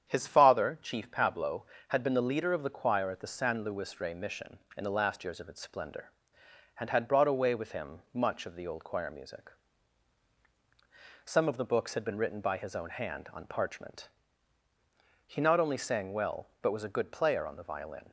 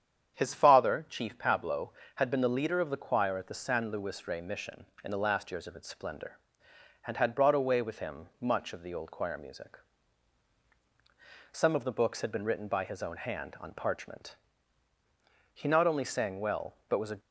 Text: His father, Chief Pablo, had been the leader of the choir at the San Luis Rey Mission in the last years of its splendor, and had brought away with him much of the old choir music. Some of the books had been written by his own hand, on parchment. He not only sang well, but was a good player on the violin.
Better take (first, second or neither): first